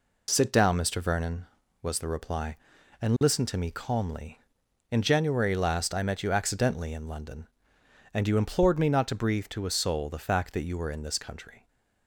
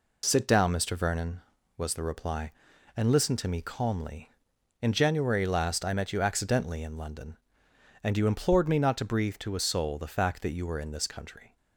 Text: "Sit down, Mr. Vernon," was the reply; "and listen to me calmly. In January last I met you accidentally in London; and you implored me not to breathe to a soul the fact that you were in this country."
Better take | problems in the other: neither | none

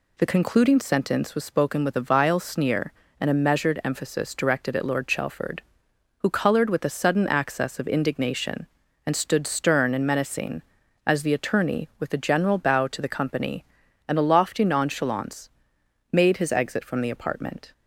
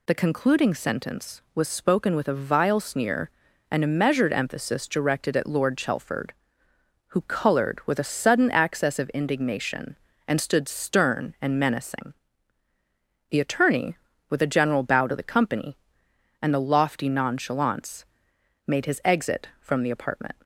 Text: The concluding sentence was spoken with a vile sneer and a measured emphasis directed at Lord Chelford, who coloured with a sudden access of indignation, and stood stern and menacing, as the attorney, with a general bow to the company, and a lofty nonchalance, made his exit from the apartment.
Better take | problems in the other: first | skips "as"; at 12.7 s

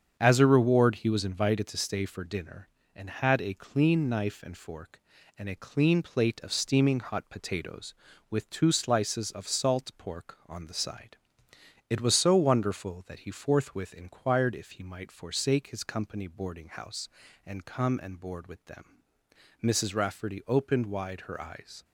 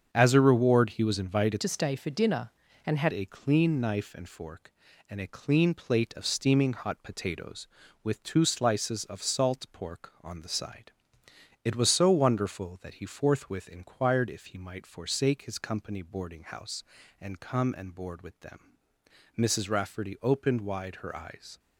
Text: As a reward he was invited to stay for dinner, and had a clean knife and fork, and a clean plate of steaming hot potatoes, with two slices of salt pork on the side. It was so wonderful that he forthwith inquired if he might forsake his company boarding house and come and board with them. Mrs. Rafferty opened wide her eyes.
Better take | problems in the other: first | starts louder than the rest; strong; until 1.1 s; 7.5 dB; strong in the first // changes voice from "to" to "had"; from 1.6 to 3.1 s; 1.5 s long

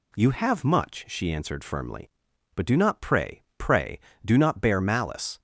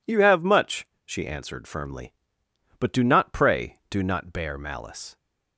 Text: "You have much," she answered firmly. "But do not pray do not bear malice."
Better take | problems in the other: second | says "pray" twice; at 3.5 s

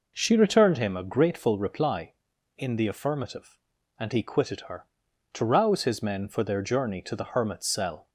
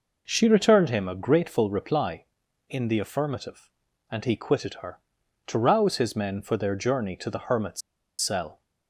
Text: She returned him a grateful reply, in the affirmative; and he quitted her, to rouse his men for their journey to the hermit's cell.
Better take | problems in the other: first | pauses between "hermit's" and "cell"; at 7.8 s; 0.40 s long

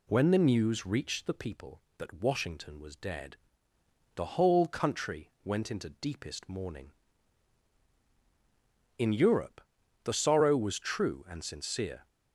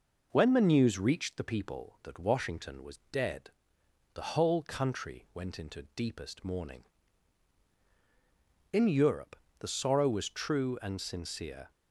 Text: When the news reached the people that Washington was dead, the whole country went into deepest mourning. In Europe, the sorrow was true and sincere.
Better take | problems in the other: neither | none

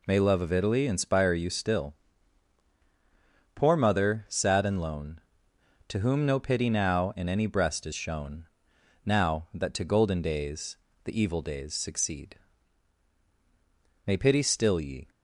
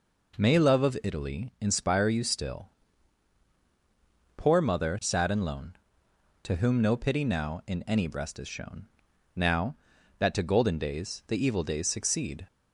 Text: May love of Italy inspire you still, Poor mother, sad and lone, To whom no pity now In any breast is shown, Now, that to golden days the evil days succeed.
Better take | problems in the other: second | pauses between "days" and "the"; slight; at 10.7 s; 0.28 s long // goes on to say "May pity still ye"; noticeable; from 14.0 s on; 1.0 s long

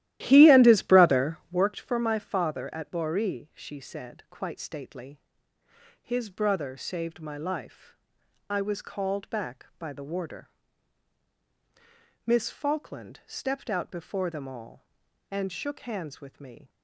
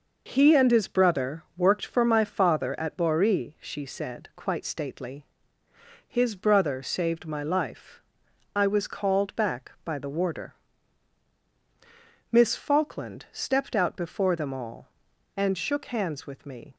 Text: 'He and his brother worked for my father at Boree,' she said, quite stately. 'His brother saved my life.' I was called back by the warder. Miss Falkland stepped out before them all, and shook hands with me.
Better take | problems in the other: second | starts louder than the rest; strong; until 1.7 s; 14.5 dB

